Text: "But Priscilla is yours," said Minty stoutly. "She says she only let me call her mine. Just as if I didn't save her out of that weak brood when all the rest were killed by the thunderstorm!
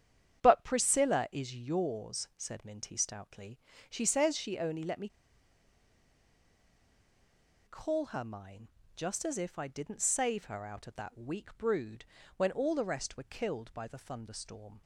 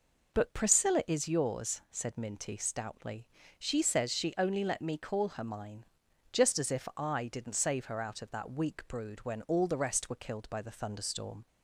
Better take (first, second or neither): second